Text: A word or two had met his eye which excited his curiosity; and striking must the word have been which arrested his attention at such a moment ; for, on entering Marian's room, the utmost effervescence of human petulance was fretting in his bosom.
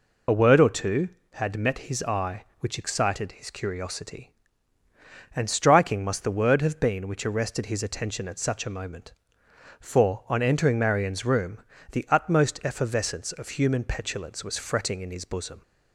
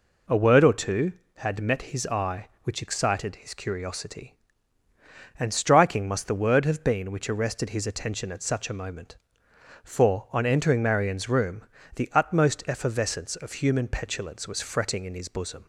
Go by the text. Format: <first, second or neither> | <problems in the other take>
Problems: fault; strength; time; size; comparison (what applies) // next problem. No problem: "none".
second | loses the start of "A"; at 0.2 s; 35 ms